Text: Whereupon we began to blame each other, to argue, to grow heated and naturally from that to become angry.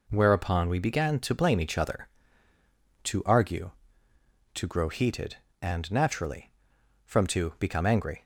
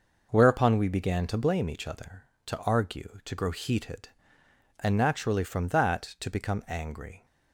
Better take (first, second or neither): second